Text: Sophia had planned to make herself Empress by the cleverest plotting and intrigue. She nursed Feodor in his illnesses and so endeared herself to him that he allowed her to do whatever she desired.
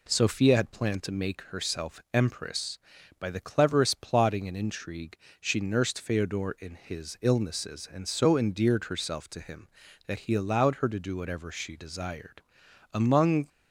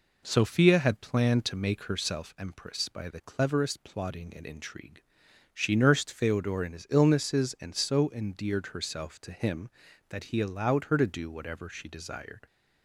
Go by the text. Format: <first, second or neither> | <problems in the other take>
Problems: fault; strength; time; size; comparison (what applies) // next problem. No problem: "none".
second | goes on to say "Among"; from 12.9 s on; 0.56 s long